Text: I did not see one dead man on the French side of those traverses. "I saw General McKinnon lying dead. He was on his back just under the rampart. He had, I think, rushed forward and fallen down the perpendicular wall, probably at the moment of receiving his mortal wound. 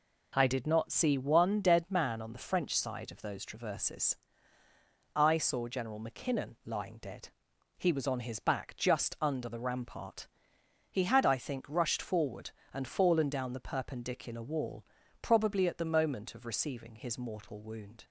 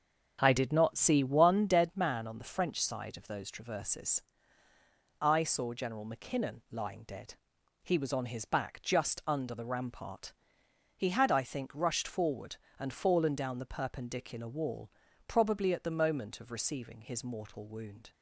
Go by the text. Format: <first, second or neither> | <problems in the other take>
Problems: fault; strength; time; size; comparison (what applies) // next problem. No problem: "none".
first | starts louder than the rest; strong; until 1.8 s; 7 dB